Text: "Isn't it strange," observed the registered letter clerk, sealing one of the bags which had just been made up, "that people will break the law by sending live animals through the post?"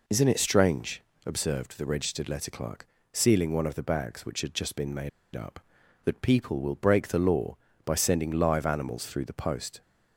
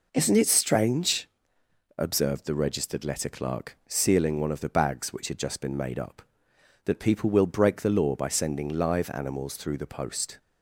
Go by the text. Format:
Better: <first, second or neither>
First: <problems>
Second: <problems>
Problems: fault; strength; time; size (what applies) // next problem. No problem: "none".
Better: second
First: pauses between "made" and "up"; slight; at 5.0 s; 0.25 s long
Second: none